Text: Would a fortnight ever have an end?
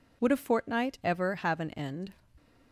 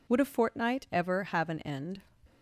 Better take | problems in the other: neither | none

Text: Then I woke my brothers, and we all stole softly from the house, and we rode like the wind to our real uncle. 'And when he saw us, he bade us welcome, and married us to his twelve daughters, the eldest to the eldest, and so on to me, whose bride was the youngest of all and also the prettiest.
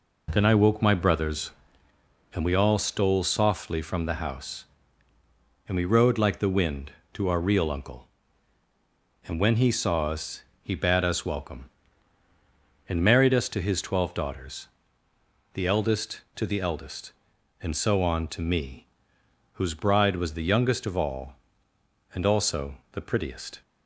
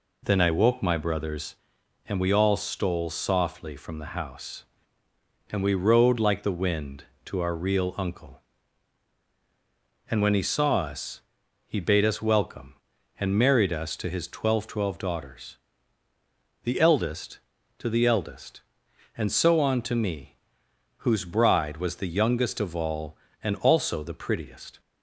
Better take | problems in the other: first | says "twelve" twice; at 14.6 s

